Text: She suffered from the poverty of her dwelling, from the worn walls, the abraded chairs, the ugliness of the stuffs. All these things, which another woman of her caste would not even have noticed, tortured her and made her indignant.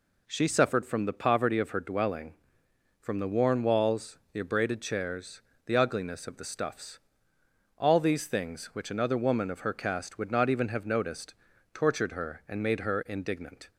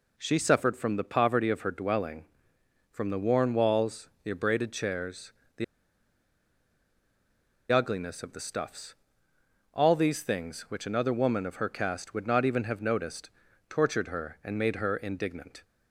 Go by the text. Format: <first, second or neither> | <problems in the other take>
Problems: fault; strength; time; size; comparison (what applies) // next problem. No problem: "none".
first | pauses between "the" and "ugliness"; strong; at 5.6 s; 2.0 s long